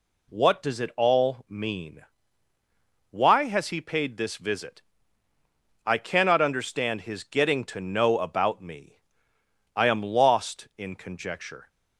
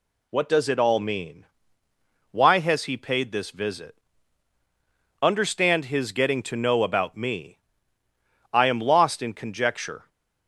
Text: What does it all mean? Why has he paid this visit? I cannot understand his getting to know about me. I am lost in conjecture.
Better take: first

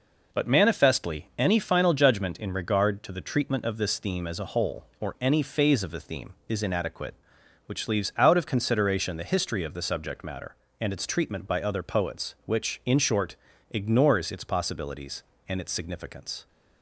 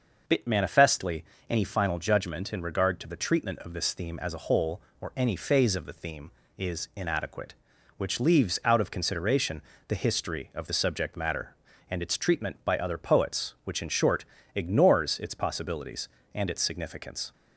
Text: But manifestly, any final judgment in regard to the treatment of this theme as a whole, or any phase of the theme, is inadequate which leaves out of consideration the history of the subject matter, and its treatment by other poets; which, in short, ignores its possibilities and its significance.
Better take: first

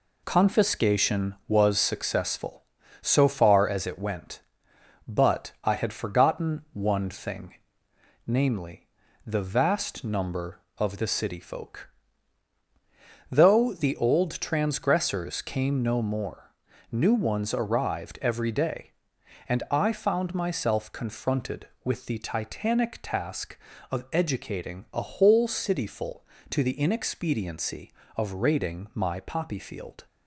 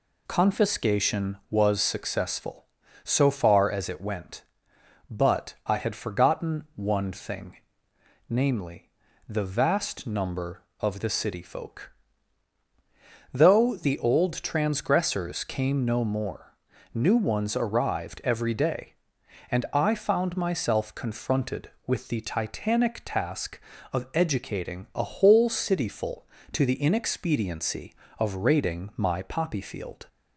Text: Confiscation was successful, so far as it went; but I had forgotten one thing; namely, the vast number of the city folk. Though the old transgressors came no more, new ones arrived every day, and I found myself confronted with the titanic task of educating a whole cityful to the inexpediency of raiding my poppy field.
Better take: second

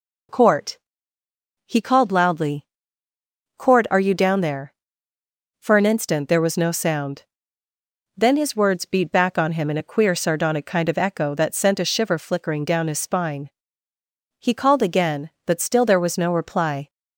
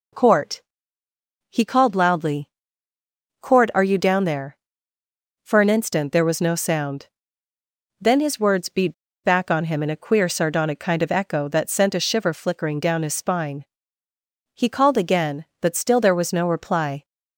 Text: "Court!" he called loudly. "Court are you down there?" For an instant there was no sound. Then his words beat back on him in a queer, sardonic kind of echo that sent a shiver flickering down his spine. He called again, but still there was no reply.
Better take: first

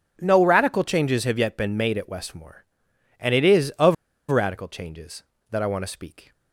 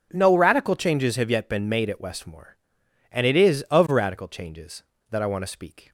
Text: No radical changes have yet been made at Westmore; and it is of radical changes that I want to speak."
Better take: second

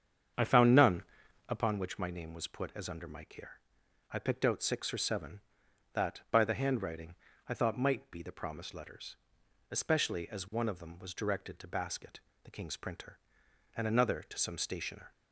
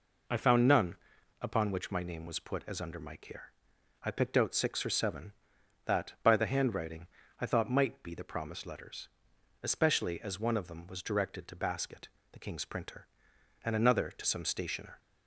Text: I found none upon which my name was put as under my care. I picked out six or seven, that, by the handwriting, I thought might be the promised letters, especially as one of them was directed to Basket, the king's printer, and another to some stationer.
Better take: second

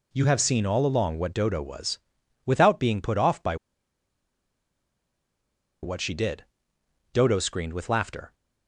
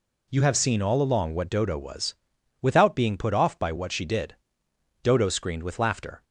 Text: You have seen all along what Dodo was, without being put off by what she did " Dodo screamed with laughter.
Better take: second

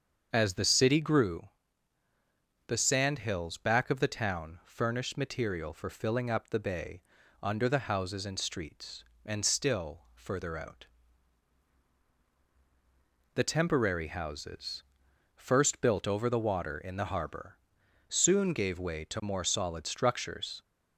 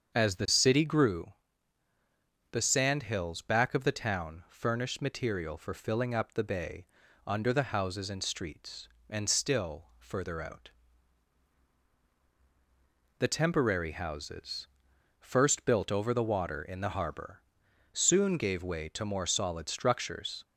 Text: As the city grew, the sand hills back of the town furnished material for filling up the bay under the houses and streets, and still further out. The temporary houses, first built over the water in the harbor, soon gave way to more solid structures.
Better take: neither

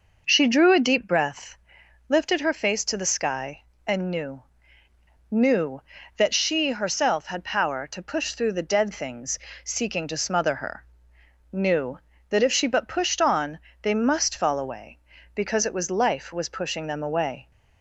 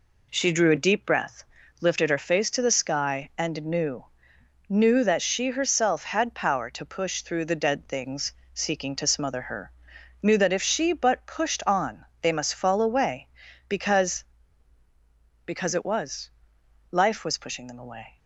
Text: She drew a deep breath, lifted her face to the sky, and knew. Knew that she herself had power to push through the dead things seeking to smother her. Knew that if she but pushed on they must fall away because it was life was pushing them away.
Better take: first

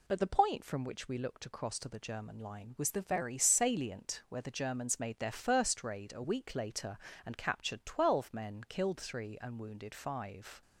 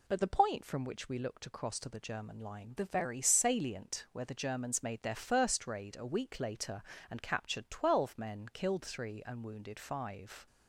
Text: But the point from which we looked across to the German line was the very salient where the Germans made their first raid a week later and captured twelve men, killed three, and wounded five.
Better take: first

